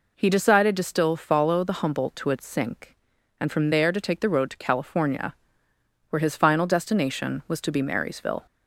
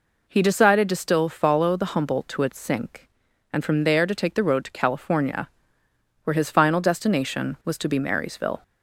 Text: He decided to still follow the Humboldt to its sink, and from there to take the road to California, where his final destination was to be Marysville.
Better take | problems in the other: neither | none

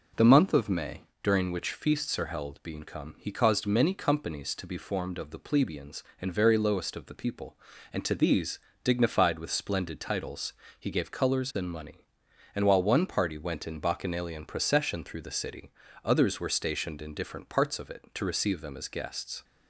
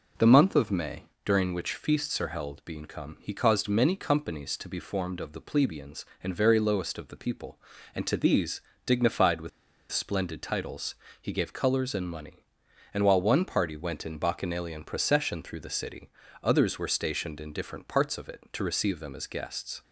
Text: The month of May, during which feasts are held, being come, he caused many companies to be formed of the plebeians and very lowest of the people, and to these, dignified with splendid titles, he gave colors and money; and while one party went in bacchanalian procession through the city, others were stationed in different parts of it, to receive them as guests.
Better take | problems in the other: first | pauses between "with" and "splendid"; at 9.4 s; 0.42 s long

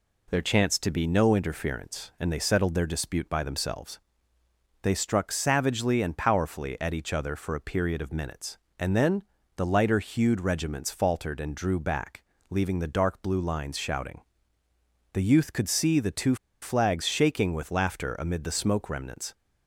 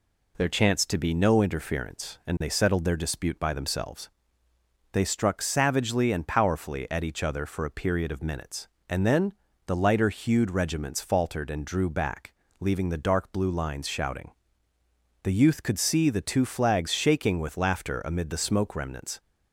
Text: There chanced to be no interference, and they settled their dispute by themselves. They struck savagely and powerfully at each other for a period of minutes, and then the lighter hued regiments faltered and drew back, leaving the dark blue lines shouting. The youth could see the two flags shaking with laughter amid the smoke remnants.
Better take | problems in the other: second | pauses between "then" and "the"; slight; at 9.2 s; 0.34 s long; slight in the second // pauses between "two" and "flags"; slight; at 16.3 s; 0.27 s long

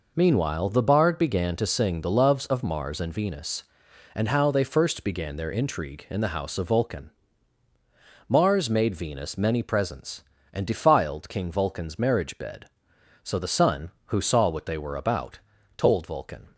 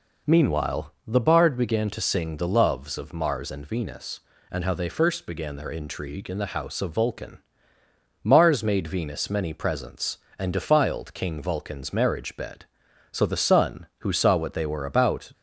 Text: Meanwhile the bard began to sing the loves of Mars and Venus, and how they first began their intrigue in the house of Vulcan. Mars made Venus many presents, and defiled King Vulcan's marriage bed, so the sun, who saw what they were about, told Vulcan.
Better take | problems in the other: first | stops before "told Vulcan"; at 15.3 s

